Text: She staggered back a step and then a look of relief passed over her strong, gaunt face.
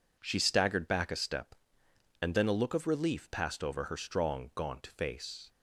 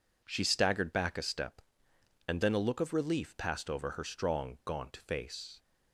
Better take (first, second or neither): neither